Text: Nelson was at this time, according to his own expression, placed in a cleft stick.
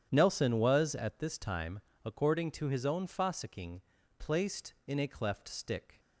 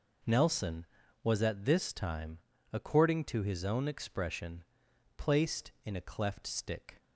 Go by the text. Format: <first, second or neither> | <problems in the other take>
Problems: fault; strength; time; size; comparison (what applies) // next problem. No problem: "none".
second | starts louder than the rest; strong; until 1.1 s; 9.5 dB // says "fossicking" for "expression"; at 3.0 s